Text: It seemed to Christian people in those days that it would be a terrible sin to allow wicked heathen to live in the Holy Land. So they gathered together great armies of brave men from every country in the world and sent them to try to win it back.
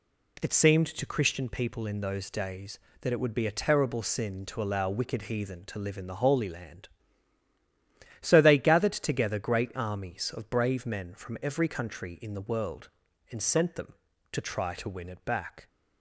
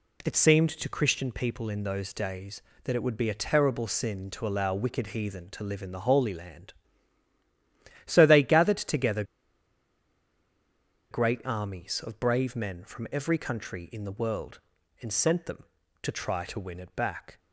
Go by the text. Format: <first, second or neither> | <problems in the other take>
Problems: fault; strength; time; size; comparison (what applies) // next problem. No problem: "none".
first | pauses between "together" and "great"; strong; at 9.2 s; 1.8 s long